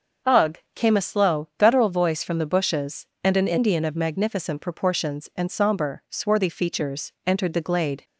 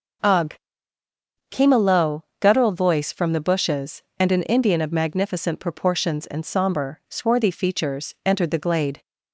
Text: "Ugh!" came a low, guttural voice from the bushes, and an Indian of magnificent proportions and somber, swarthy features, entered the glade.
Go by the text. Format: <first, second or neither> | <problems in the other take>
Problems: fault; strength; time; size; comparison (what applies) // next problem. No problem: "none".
second | starts louder than the rest; until 1.4 s; 6 dB // says "slow" for "low"; at 1.0 s